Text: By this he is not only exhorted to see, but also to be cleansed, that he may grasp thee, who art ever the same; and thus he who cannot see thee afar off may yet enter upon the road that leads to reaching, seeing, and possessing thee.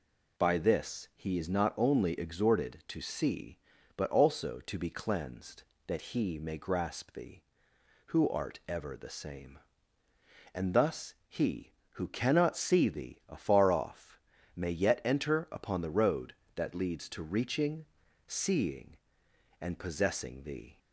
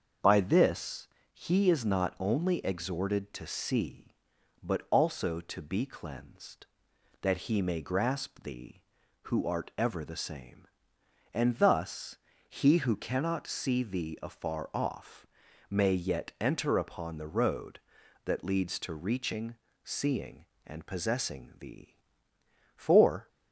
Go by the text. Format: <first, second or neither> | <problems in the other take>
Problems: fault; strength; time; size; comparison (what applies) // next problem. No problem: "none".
first | starts louder than the rest; until 1.4 s; 6.5 dB // pauses between "this" and "he"; slight; at 1.0 s; 0.26 s long // pauses between "thus" and "he"; slight; at 12.1 s; 0.30 s long // pauses between "off" and "may"; noticeable; at 15.2 s; 0.46 s long; slight in the first // goes on to say "For"; from 22.7 s on; 0.52 s long